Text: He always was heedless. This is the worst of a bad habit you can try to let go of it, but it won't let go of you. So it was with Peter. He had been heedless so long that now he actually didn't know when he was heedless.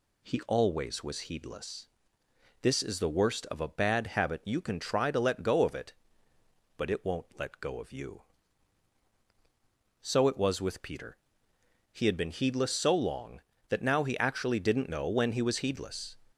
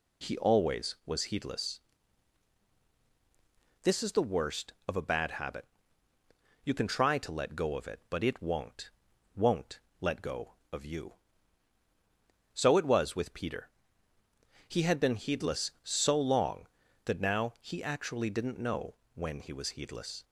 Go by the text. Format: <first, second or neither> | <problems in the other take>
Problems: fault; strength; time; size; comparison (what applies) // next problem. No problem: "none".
first | pauses between "habit" and "you"; noticeable; at 5.6 s; 0.98 s long // says "won't" twice; at 9.3 s // pauses between "know" and "when"; slight; at 18.9 s; 0.22 s long